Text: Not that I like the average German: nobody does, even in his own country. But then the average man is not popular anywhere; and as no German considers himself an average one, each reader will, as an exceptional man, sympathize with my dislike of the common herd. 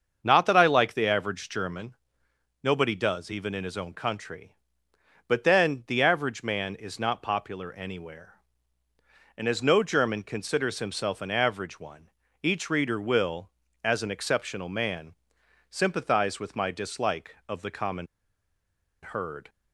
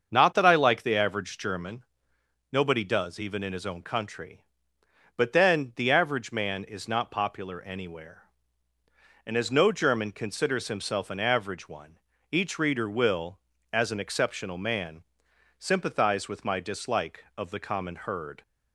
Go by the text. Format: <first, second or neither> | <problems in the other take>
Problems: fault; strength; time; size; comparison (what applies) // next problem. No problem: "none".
second | starts louder than the rest; until 1.2 s; 6.5 dB; also in the second // pauses between "common" and "herd"; noticeable; at 18.0 s; 0.96 s long